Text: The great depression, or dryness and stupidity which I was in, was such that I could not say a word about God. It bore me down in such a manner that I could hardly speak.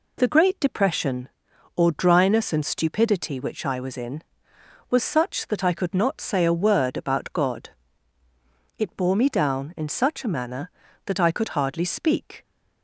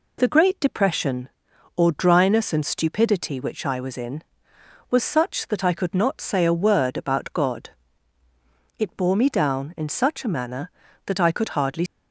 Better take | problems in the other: first | stops before "speak"; at 11.8 s

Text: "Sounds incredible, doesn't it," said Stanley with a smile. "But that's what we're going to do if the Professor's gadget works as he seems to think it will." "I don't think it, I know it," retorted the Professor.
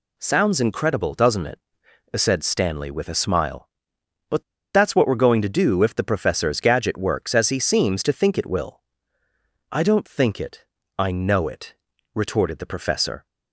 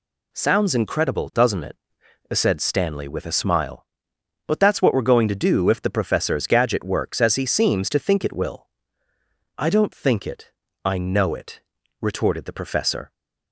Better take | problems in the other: second | pauses between "But" and "that's"; slight; at 4.4 s; 0.33 s long

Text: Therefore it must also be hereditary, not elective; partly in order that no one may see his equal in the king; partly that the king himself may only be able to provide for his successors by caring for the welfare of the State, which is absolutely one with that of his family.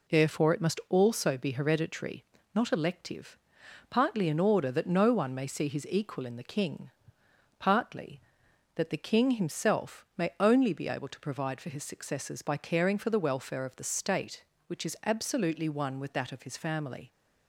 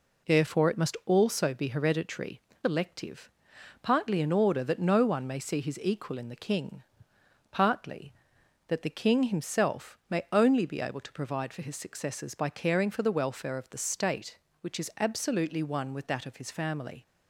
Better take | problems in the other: first | skips "not"; at 2.5 s

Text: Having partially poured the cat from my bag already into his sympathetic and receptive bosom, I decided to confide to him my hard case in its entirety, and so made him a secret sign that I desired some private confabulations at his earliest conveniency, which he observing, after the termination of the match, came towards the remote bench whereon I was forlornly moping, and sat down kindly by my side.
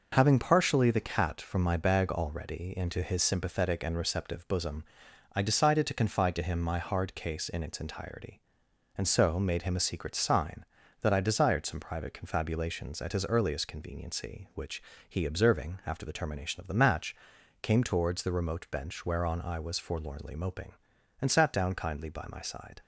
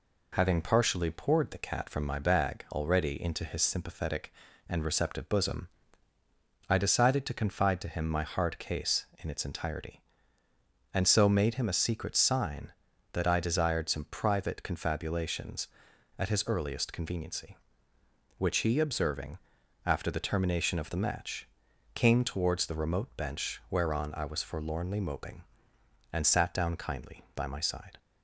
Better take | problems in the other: second | skips "poured"; at 0.9 s // pauses between "which" and "he"; slight; at 14.8 s; 0.26 s long

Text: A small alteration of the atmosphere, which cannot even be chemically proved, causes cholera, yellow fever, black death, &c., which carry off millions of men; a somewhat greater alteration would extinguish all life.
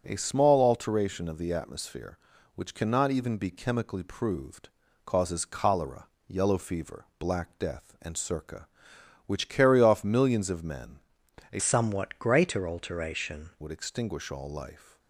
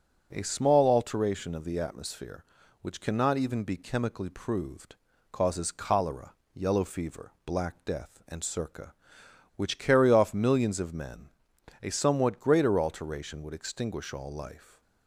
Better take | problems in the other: second | starts louder than the rest; until 1.0 s; 6 dB; also in the second // changes voice from "somewhat" to "alteration"; from 11.5 to 13.5 s; 2.0 s long

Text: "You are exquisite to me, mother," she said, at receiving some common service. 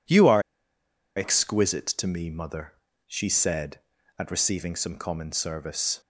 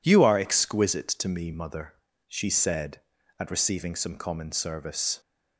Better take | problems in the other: second | pauses between "are" and "exquisite"; noticeable; at 0.3 s; 0.76 s long

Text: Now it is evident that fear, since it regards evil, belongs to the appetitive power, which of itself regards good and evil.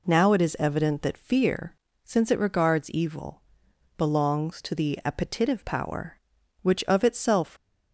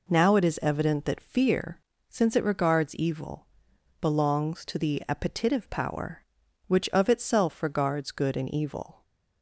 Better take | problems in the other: second | stops before "regards good and evil"; at 7.5 s

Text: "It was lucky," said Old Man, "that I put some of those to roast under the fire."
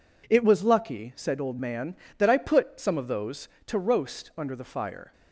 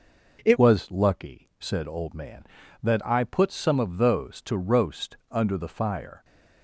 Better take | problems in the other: first | changes voice at "was"; from 0.5 s on; 5.7 s long

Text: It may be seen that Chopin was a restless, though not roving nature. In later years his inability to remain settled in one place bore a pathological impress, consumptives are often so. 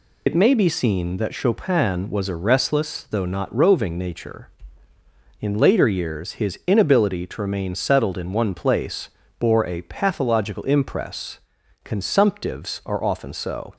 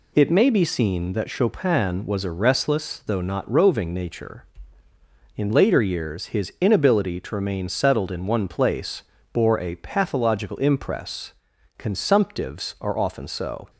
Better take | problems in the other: second | loses the start of "It"; at 0.2 s; 75 ms // pauses between "place" and "bore"; slight; at 9.0 s; 0.30 s long; slight in the second

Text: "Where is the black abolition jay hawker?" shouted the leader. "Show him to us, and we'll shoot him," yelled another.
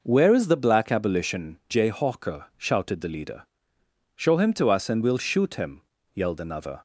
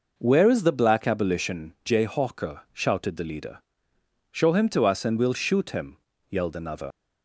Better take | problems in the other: first | leaves "another" unfinished; at 6.9 s; 65 ms

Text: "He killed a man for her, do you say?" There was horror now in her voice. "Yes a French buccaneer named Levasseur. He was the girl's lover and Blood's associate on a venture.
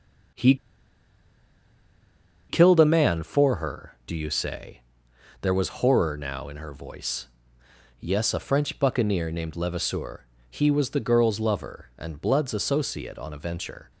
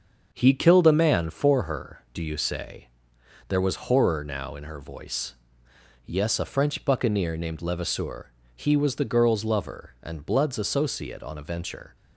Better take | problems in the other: second | starts louder than the rest; until 3.3 s; 7 dB; also in the second // pauses between "He" and "killed"; strong; at 0.5 s; 1.9 s long

